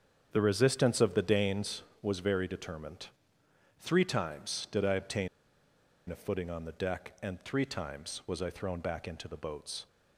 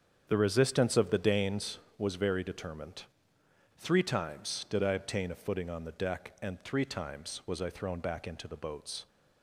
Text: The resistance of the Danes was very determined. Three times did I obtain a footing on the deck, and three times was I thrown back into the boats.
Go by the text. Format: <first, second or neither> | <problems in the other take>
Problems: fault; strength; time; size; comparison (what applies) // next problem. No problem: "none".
second | starts louder than the rest; strong; until 1.3 s; 8 dB; strong in the second // pauses between "obtain" and "a"; noticeable; at 5.2 s; 0.80 s long